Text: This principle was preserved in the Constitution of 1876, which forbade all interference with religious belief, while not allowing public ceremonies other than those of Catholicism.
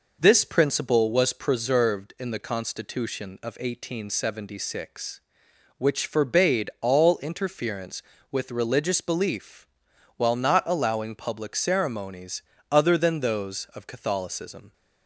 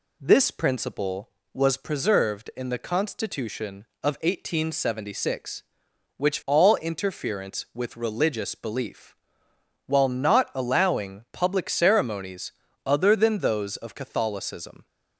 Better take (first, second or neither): first